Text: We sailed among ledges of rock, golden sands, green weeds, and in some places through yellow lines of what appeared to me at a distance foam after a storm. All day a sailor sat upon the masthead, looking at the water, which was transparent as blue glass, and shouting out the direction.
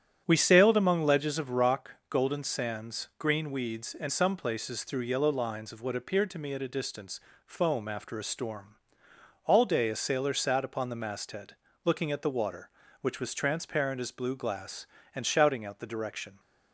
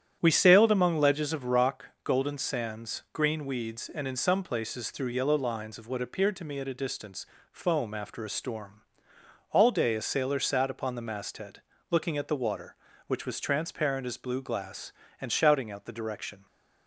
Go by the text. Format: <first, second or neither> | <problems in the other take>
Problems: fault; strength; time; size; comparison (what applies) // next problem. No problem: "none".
second | starts louder than the rest; strong; until 1.2 s; 9.5 dB; strong in the second // skips "in"; at 4.0 s // pauses between "distance" and "foam"; slight; at 7.1 s; 0.28 s long; slight in the second